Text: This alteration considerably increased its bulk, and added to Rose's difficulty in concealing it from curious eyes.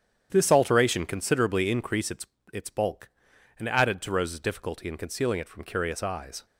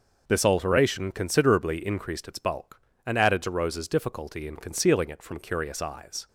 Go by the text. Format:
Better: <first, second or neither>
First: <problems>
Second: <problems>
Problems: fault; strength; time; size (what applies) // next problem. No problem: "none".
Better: second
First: starts louder than the rest; strong; until 1.3 s; 8.5 dB // says "its" twice; at 2.5 s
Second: none